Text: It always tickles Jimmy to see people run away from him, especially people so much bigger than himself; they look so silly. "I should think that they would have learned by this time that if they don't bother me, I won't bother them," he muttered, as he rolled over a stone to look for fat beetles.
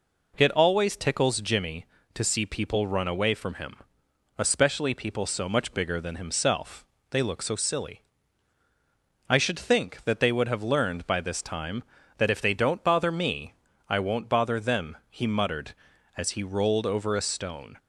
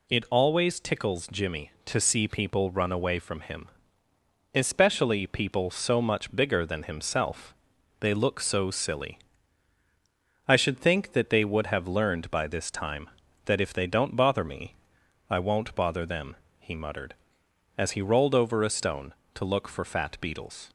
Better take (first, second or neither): second